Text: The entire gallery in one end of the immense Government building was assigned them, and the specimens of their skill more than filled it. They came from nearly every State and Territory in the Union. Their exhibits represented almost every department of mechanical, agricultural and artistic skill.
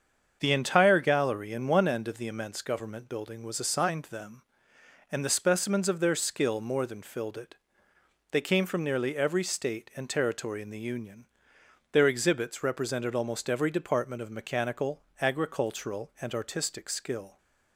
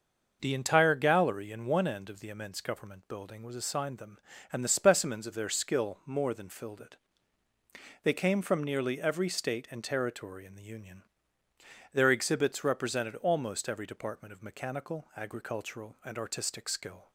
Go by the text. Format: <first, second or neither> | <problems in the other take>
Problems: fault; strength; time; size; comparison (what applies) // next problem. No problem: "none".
neither | starts louder than the rest; the same in both